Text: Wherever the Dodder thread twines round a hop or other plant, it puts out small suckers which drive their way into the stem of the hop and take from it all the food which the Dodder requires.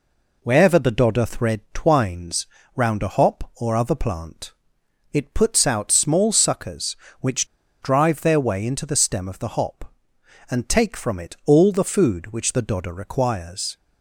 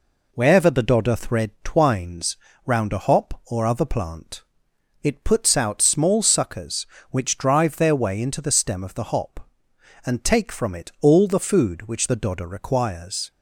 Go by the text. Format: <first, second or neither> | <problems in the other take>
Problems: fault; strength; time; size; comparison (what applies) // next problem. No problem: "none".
second | pauses between "twines" and "round"; slight; at 2.4 s; 0.28 s long; slight in the second // pauses between "which" and "drive"; at 7.4 s; 0.36 s long